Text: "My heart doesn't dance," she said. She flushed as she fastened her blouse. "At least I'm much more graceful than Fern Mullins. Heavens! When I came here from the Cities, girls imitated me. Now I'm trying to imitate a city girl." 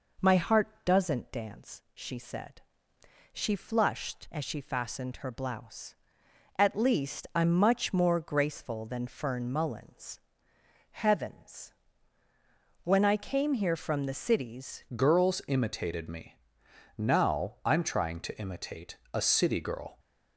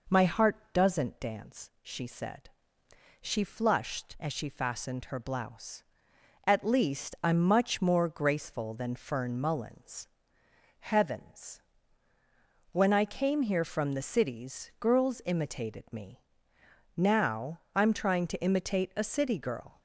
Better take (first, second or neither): second